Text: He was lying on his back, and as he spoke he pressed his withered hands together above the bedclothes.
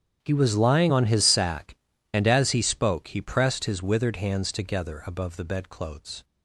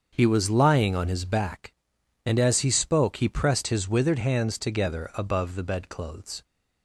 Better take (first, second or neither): second